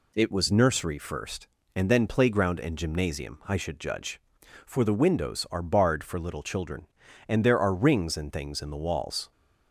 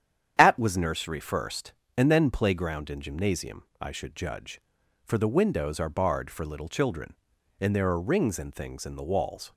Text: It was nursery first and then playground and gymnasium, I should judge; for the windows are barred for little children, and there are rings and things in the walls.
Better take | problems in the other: first | starts louder than the rest; strong; until 1.3 s; 9.5 dB // says "At" for "It"; at 0.3 s

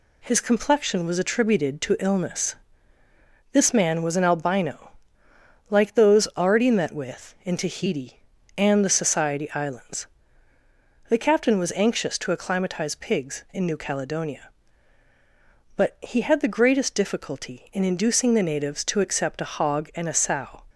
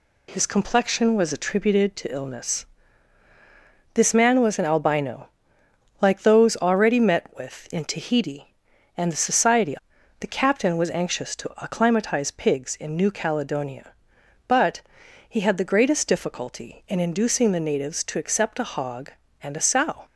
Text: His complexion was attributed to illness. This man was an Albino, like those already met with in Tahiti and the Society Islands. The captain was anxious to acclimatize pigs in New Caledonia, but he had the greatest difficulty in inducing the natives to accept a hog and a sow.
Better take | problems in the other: first | skips "Islands"; at 9.9 s // pauses between "but" and "he"; noticeable; at 14.7 s; 0.48 s long

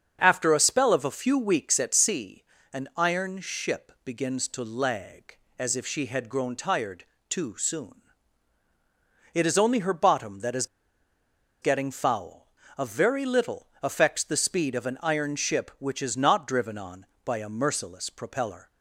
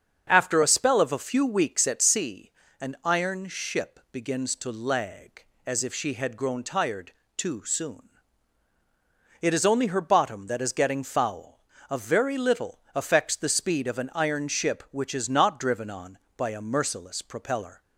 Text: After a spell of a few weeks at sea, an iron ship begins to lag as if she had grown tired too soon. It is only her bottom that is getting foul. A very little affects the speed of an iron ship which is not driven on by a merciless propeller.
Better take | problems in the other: second | starts louder than the rest; strong; until 1.2 s; 7 dB; also in the second // pauses between "tired" and "too"; slight; at 7.0 s; 0.24 s long; slight in the second // pauses between "is" and "getting"; noticeable; at 10.6 s; 0.96 s long // pauses between "little" and "affects"; slight; at 13.6 s; 0.16 s long; slight in the second

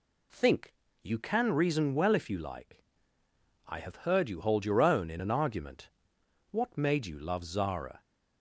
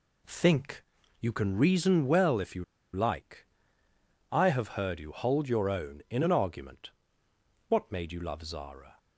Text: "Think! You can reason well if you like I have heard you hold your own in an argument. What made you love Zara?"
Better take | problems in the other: first | pauses between "you" and "like"; slight; at 2.6 s; 0.29 s long // pauses between "like" and "I"; noticeable; at 3.4 s; 0.82 s long; noticeable in the first

